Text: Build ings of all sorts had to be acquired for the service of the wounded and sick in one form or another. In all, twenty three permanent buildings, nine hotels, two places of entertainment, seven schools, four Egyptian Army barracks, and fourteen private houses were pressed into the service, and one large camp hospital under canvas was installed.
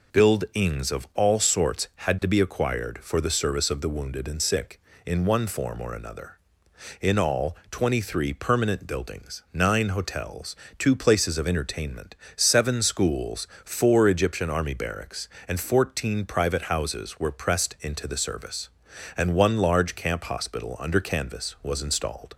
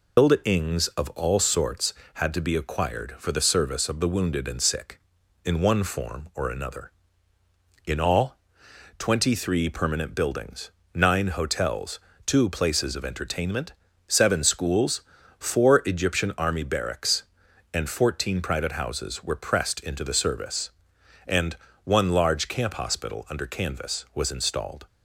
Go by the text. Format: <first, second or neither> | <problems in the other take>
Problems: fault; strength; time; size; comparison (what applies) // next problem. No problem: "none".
first | loses the start of "Build"; at 0.1 s; 130 ms // pauses between "and" and "one"; slight; at 21.5 s; 0.30 s long